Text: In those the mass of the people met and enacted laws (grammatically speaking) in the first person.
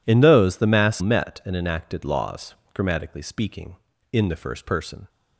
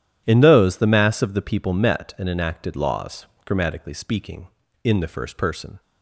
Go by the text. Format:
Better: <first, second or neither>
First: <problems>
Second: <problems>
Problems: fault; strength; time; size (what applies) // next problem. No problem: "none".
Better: second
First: skips "of the people"; at 1.0 s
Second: none